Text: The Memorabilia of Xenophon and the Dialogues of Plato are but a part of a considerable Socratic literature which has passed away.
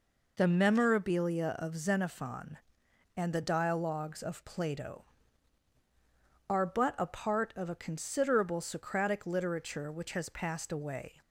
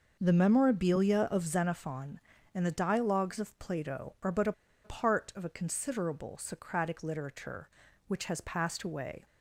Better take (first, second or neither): first